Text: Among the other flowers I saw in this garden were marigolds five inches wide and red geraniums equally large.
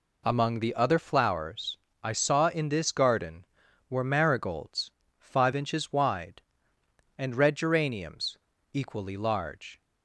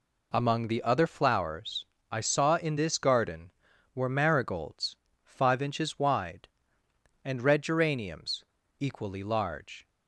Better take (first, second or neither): neither